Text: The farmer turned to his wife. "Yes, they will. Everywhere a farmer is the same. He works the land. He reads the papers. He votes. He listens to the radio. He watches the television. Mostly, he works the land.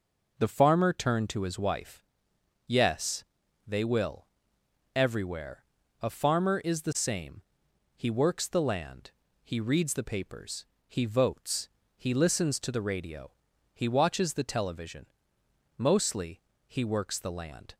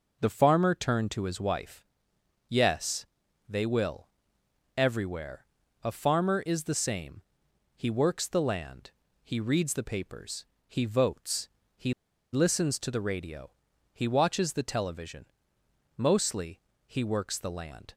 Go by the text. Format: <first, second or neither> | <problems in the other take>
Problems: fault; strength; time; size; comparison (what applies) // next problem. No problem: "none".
first | pauses between "Everywhere" and "a"; at 5.4 s; 0.38 s long; also in the first // pauses between "He" and "listens"; at 11.9 s; 0.40 s long